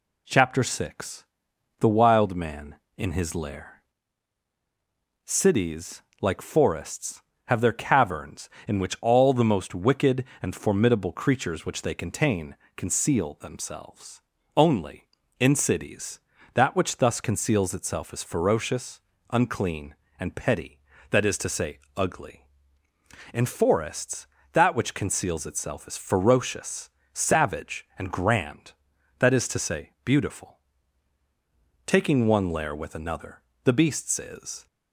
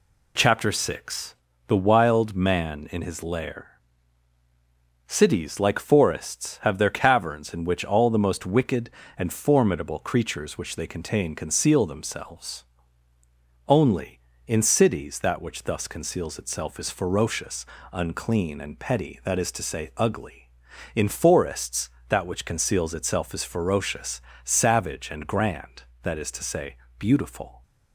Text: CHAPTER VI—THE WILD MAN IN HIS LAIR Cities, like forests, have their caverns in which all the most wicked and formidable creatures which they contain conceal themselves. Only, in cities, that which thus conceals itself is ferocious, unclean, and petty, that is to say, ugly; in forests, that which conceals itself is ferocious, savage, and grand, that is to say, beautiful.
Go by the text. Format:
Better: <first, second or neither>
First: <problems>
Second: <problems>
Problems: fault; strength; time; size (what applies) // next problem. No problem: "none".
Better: second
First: pauses between "LAIR" and "Cities"; strong; at 3.8 s; 1.4 s long // pauses between "contain" and "conceal"; slight; at 12.5 s; 0.18 s long // goes on to say "Taking one lair with another the beast's is"; strong; from 31.8 s on; 2.8 s long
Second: pauses between "LAIR" and "Cities"; strong; at 3.7 s; 1.2 s long